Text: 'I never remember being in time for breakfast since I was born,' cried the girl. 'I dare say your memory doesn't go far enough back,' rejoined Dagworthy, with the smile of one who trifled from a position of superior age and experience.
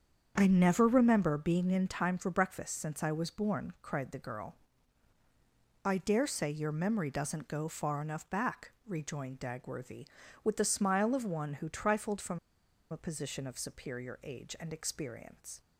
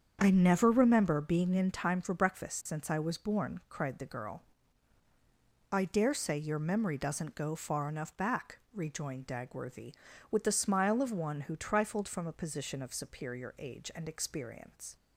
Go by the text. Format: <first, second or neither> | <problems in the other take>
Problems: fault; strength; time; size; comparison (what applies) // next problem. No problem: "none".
second | starts louder than the rest; strong; until 1.3 s; 7.5 dB; strong in the second // pauses between "from" and "a"; noticeable; at 12.3 s; 0.52 s long